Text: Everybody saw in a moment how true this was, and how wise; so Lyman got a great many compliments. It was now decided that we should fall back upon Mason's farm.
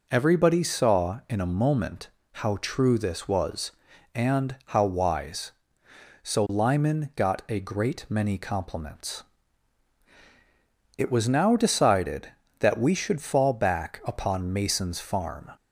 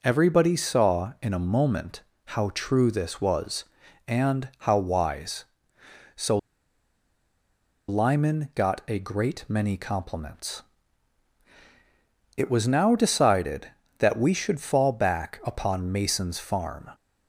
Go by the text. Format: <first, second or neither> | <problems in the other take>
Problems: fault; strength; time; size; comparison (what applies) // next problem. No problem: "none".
first | pauses between "moment" and "how"; slight; at 2.0 s; 0.24 s long; slight in the first // pauses between "so" and "Lyman"; strong; at 6.3 s; 1.5 s long